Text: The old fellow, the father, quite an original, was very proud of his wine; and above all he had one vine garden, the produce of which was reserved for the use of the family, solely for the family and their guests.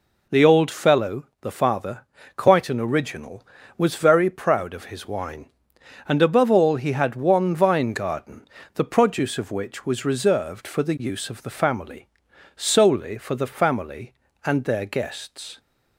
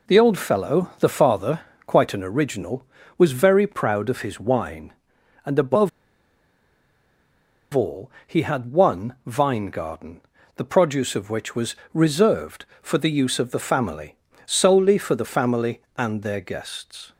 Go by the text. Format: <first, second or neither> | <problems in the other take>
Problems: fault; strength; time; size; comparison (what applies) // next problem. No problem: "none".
first | pauses between "above" and "all"; strong; at 5.8 s; 1.8 s long // pauses between "all" and "he"; slight; at 8.1 s; 0.16 s long // pauses between "was" and "reserved"; slight; at 11.7 s; 0.20 s long